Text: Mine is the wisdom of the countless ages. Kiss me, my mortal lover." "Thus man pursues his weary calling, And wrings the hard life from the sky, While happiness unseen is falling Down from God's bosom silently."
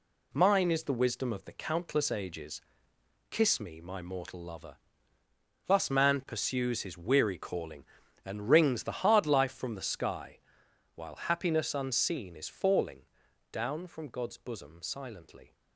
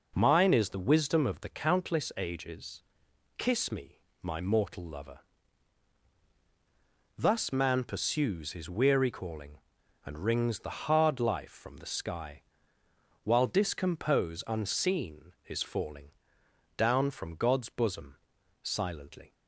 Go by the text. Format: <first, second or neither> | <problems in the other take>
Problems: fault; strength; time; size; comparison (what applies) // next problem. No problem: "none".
first | says "discompose" for "happiness"; at 13.4 s // pauses between "falling" and "Down"; noticeable; at 16.1 s; 0.66 s long; noticeable in the first // pauses between "bosom" and "silently"; at 18.1 s; 0.44 s long